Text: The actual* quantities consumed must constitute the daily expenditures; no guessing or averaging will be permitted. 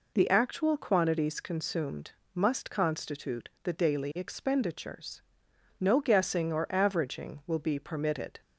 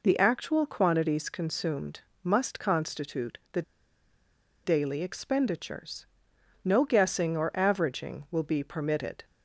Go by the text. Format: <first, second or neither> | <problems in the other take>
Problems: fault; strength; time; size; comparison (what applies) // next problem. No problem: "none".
first | pauses between "consumed" and "must"; slight; at 2.0 s; 0.20 s long; slight in the first // pauses between "the" and "daily"; at 3.6 s; 1.0 s long